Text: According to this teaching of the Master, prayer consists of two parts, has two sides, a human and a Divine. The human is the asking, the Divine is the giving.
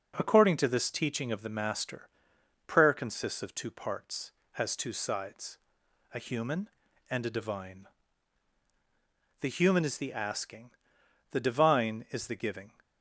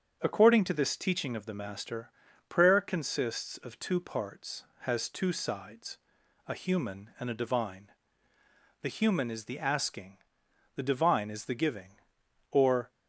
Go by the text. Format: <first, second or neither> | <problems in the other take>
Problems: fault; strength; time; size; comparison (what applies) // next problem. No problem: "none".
first | starts louder than the rest; strong; until 1.2 s; 7.5 dB // goes on to say "Or"; slight; from 12.5 s on; 0.38 s long